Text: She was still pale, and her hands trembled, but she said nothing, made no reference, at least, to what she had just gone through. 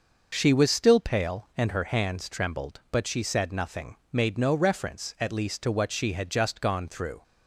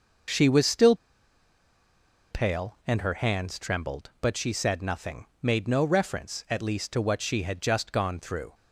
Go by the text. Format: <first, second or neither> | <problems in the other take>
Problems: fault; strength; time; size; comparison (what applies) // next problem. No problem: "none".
first | pauses between "still" and "pale"; strong; at 0.9 s; 1.3 s long